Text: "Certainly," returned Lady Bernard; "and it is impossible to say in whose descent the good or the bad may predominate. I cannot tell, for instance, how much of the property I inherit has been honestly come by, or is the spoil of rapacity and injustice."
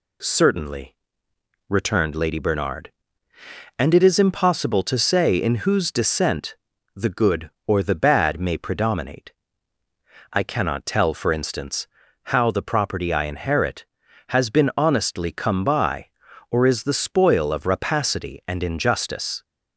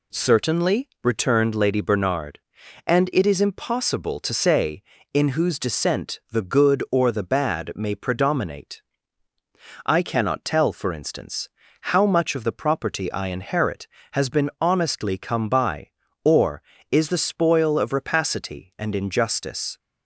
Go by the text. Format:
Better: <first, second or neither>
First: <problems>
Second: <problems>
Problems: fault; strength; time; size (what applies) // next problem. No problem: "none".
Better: second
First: pauses between "descent" and "the"; slight; at 6.5 s; 0.36 s long // skips "much of"; at 12.5 s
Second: none